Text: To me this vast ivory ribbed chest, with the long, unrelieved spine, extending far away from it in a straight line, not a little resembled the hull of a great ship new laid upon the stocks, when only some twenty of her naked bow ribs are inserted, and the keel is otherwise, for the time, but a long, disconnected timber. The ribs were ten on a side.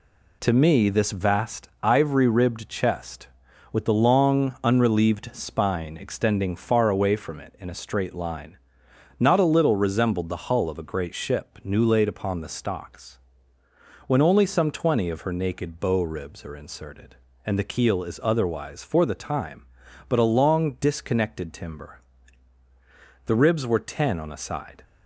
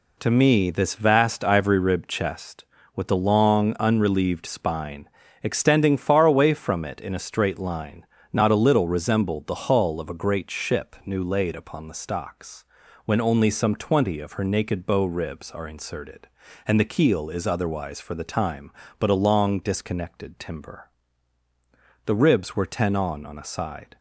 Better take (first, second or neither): first